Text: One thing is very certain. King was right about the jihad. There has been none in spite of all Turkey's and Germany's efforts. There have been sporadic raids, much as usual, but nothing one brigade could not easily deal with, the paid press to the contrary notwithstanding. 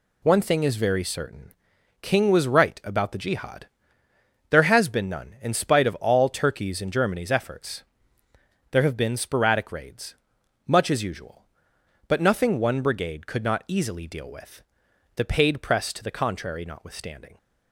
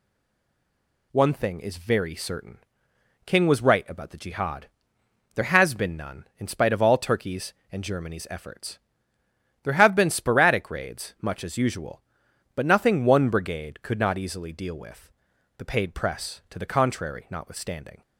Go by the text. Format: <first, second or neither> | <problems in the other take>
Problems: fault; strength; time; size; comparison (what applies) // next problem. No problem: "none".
first | stays silent before the first word; until 1.1 s; 1.1 s long